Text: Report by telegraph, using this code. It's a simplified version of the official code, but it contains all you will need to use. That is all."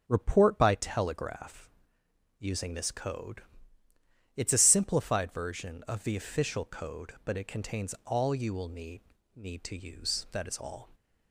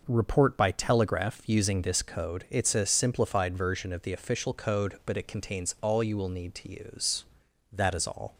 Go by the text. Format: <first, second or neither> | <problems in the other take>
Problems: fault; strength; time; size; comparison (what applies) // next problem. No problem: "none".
second | starts louder than the rest; strong; until 1.0 s; 9 dB // says "need" twice; at 9.3 s